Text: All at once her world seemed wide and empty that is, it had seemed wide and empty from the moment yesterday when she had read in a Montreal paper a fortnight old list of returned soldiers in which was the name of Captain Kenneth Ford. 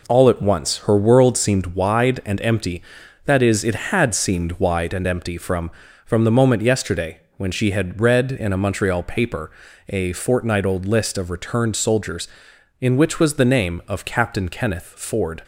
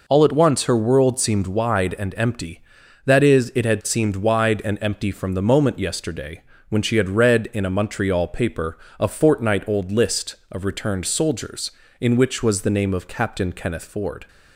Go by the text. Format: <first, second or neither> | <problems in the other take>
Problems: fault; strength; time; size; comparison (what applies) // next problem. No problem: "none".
second | says "from" twice; at 6.0 s // pauses between "yesterday" and "when"; slight; at 7.1 s; 0.18 s long; slight in the second // pauses between "paper" and "a"; at 9.5 s; 0.38 s long; slight in the second